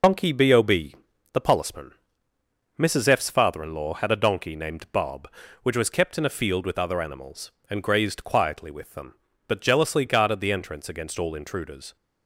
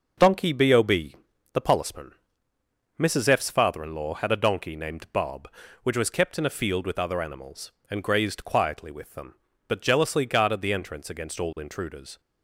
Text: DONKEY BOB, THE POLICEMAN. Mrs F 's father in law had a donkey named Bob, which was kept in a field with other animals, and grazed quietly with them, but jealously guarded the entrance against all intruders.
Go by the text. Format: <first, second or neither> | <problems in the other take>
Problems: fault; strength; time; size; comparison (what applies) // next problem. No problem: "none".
second | loses the start of "DONKEY"; at 0.0 s; 55 ms